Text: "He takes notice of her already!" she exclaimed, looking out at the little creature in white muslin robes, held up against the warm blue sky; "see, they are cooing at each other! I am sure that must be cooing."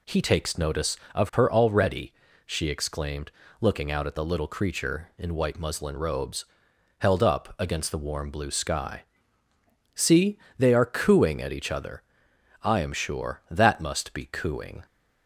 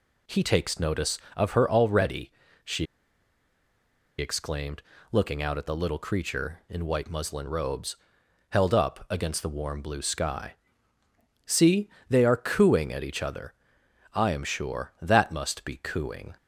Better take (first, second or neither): first